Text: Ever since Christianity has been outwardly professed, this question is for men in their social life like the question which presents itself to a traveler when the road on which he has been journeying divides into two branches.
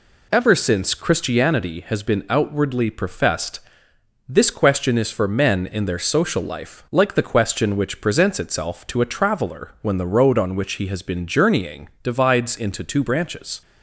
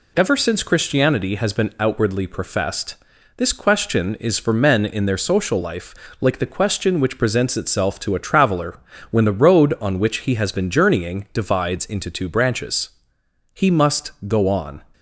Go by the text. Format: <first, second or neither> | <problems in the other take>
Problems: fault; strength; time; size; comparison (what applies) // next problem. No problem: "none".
first | pauses between "life" and "like"; slight; at 5.9 s; 0.26 s long // pauses between "traveler" and "when"; slight; at 8.7 s; 0.32 s long // goes on to say "He must go on"; noticeable; from 13.5 s on; 1.2 s long